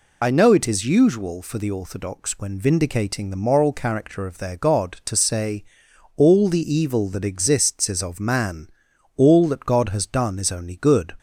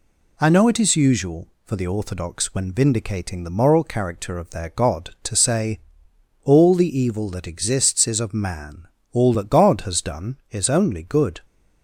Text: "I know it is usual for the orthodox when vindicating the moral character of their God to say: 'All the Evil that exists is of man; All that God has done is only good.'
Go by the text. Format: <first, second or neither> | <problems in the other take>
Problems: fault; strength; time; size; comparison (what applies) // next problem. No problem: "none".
second | loses the start of "I"; at 0.2 s; 35 ms